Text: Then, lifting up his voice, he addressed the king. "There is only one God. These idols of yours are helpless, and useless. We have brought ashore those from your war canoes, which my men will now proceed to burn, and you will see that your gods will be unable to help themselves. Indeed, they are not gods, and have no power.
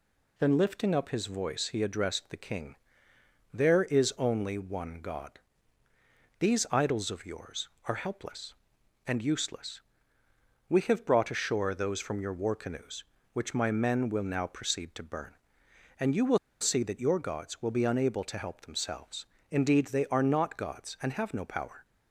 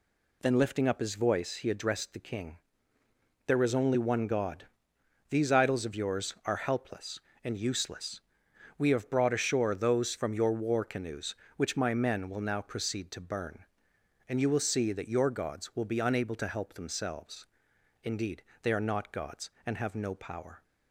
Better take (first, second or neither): second